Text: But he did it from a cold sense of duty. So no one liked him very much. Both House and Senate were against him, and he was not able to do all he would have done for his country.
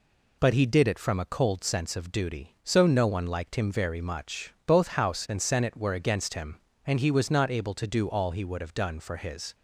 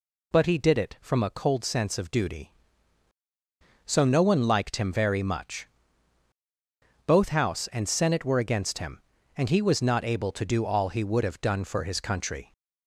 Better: second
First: stops before "country"; at 9.5 s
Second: none

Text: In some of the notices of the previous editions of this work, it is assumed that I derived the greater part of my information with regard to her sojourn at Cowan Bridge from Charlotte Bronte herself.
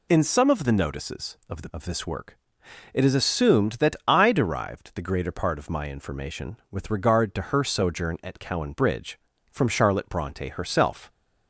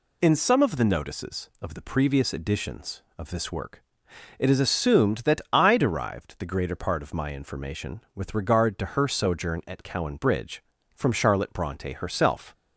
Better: second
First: skips "previous editions"; at 1.6 s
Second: none

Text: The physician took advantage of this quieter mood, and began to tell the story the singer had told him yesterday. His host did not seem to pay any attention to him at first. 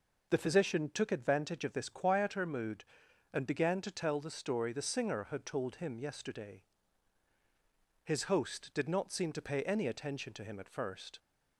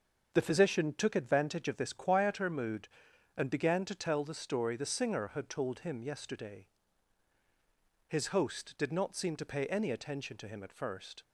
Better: first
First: none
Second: gets quieter; throughout; 6.5 dB

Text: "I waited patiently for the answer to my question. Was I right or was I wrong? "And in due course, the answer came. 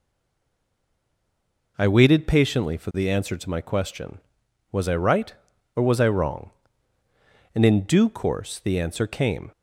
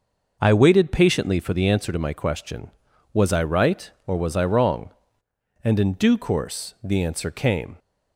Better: second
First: stays silent before the first word; noticeable; until 1.7 s; 1.7 s long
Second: none

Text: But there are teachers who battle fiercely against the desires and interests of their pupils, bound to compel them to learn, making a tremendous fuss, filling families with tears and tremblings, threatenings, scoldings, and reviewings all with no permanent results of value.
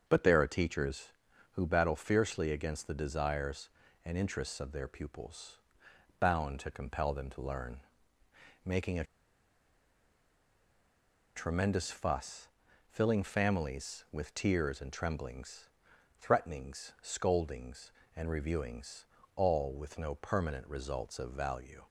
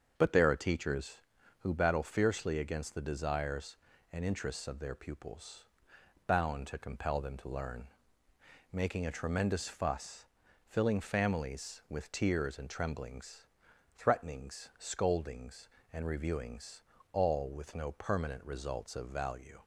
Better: second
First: starts louder than the rest; until 1.0 s; 6.5 dB // pauses between "a" and "tremendous"; strong; at 9.0 s; 2.3 s long // pauses between "reviewings" and "all"; slight; at 19.0 s; 0.30 s long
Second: starts louder than the rest; until 1.1 s; 6.5 dB // pauses between "reviewings" and "all"; slight; at 16.8 s; 0.30 s long

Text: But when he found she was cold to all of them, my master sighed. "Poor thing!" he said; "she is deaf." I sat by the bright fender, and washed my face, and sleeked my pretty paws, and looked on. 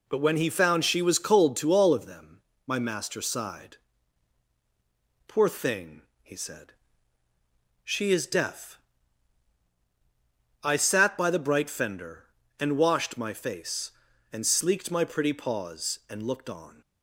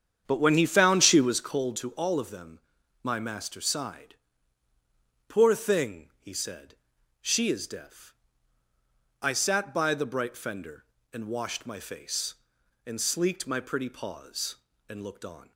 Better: first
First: none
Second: starts louder than the rest; strong; until 1.6 s; 8.5 dB

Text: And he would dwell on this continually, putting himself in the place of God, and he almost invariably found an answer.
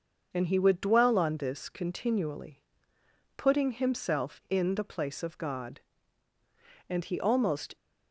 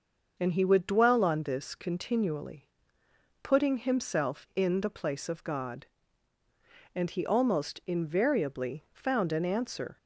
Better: second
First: starts louder than the rest; noticeable; until 1.3 s; 6 dB // stops before "invariably found an answer"; at 7.7 s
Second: starts louder than the rest; noticeable; until 1.3 s; 6 dB

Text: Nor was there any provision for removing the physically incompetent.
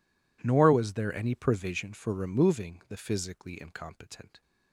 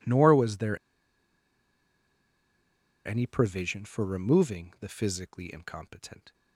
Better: first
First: none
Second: pauses between "there" and "any"; strong; at 0.7 s; 2.2 s long

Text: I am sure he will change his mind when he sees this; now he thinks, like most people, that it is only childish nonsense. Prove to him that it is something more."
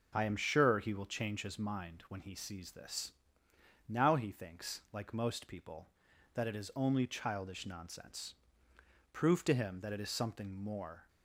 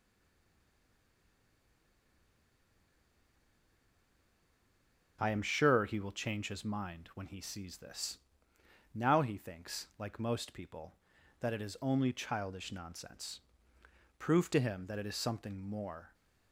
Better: first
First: none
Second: stays silent before the first word; strong; until 5.1 s; 5.1 s long

